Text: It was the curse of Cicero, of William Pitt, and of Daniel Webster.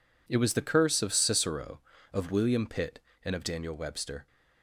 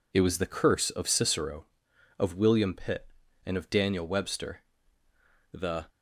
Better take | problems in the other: first | goes on to say "The"; slight; from 5.5 s on; 0.34 s long

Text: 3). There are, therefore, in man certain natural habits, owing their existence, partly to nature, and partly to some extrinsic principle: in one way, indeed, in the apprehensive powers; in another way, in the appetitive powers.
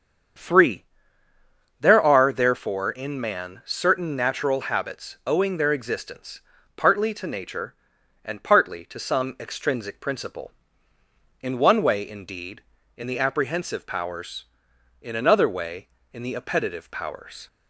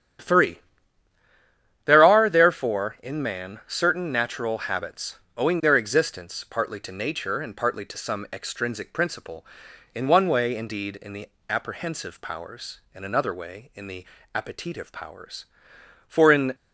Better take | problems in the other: first | starts louder than the rest; strong; until 2.4 s; 9.5 dB; strong in the first // pauses between "the" and "apprehensive"; slight; at 11.2 s; 0.22 s long // pauses between "the" and "appetitive"; slight; at 14.0 s; 0.28 s long // goes on to say "For in"; slight; from 16.0 s on; 0.48 s long

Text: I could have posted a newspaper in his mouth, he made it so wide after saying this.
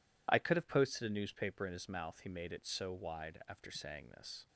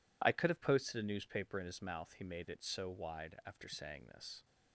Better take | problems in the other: neither | none

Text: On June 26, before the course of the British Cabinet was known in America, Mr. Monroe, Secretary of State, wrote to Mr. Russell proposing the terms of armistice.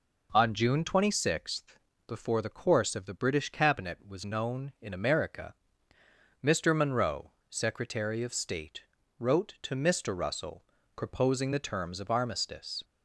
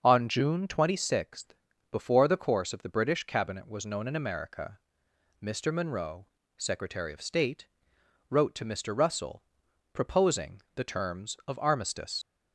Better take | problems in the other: first | starts louder than the rest; until 1.0 s; 6.5 dB // pauses between "Russell" and "proposing"; noticeable; at 9.4 s; 0.50 s long; slight in the first // leaves "armistice" unfinished; at 12.2 s; 70 ms

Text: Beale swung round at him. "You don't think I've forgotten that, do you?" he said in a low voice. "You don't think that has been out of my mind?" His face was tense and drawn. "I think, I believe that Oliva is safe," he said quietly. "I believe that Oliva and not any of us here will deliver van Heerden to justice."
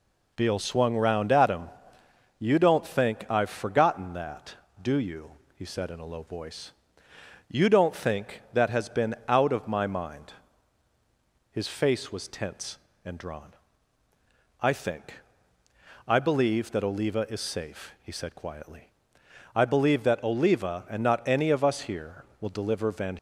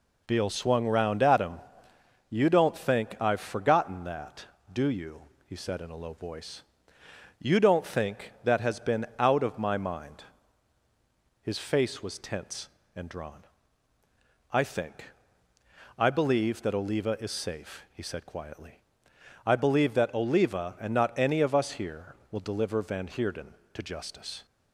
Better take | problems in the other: second | stops before "Heerden to justice"; at 23.1 s

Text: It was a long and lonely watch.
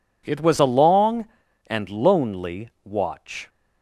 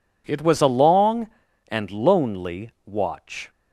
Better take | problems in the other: neither | none

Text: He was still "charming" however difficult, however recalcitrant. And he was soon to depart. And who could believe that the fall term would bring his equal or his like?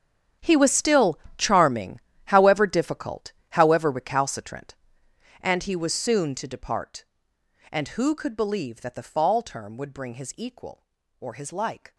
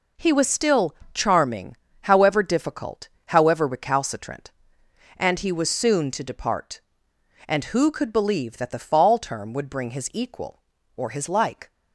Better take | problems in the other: second | gets quieter; strong; throughout; 16.5 dB // pauses between "still" and "charming"; slight; at 1.1 s; 0.18 s long; slight in the second // pauses between "charming" and "however"; slight; at 1.9 s; 0.26 s long; slight in the second

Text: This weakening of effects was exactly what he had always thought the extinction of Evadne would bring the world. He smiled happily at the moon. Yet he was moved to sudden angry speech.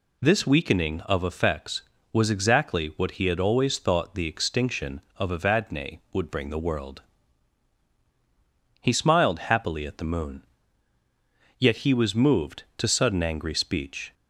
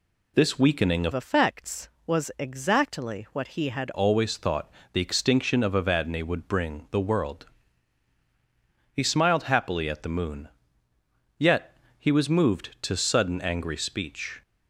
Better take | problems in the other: first | changes voice from "effects" to "had"; from 1.1 to 3.9 s; 2.8 s long // pauses between "thought" and "the"; slight; at 4.6 s; 0.24 s long // pauses between "Yet" and "he"; slight; at 11.7 s; 0.22 s long

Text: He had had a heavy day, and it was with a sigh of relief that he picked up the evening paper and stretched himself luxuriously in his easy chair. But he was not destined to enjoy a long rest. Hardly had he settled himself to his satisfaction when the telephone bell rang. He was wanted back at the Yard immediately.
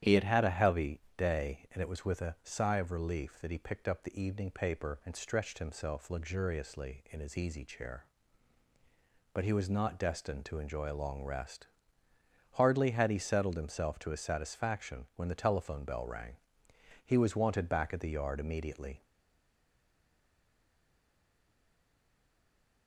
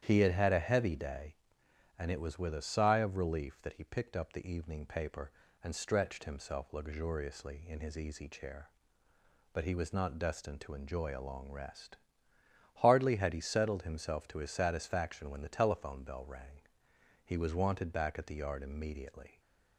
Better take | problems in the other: second | starts louder than the rest; strong; until 1.2 s; 10.5 dB; strong in the second // pauses between "heavy" and "day"; slight; at 0.9 s; 0.16 s long // stays silent after the last word; strong; from 19.0 s on; 3.8 s long

